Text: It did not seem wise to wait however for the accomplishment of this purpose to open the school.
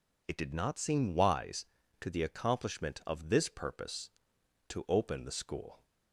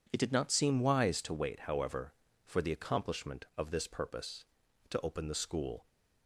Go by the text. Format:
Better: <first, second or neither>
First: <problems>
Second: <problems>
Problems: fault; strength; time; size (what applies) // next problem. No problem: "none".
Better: second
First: skips "wait however for"; at 2.0 s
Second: none